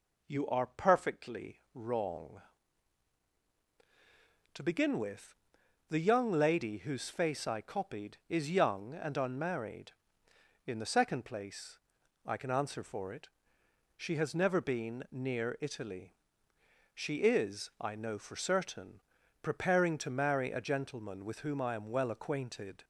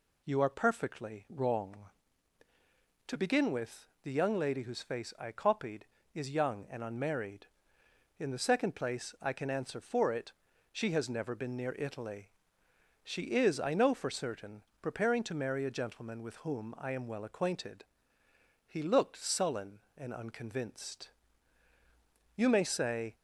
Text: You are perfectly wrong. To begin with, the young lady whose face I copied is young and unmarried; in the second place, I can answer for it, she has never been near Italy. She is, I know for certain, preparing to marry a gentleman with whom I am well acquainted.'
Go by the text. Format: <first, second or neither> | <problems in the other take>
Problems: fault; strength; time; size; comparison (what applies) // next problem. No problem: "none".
first | goes on to say "He looked sullen and unconvinced You may say"; strong; from 18.6 s on; 4.4 s long